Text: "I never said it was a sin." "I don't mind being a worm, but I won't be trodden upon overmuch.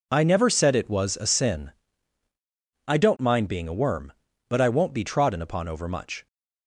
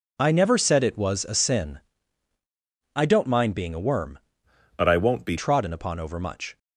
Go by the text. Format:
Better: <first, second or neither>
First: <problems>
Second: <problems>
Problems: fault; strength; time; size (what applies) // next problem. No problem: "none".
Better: first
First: none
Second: changes voice from "but" to "be"; from 4.7 to 5.3 s; 0.6 s long